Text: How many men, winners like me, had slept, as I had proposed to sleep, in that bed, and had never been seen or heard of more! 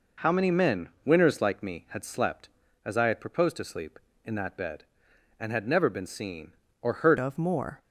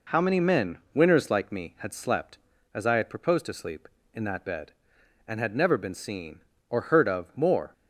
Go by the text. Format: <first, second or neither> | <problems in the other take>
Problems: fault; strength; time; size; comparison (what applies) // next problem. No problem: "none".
second | changes voice at "of"; from 7.1 s on; 0.7 s long